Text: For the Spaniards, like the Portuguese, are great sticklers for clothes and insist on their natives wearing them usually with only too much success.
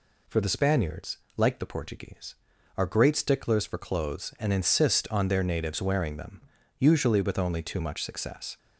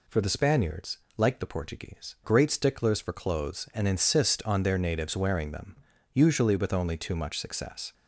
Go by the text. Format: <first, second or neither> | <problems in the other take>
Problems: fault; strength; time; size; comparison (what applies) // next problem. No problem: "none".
first | skips "are"; at 2.1 s // pauses between "them" and "usually"; at 5.7 s; 0.38 s long; also in the first